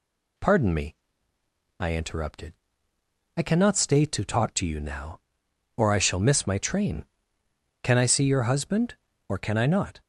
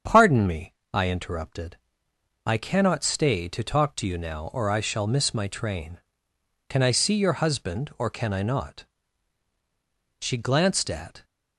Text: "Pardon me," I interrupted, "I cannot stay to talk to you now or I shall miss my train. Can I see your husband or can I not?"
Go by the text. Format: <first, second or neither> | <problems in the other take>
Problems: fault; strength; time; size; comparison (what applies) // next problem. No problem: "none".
first | starts louder than the rest; strong; until 1.2 s; 7.5 dB // goes on to say "She glanced at"; noticeable; from 10.2 s on; 1.0 s long